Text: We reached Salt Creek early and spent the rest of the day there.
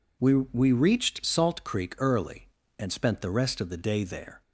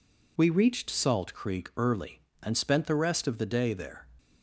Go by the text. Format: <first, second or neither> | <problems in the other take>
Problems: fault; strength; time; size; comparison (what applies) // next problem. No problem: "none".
second | says "We" twice; at 0.3 s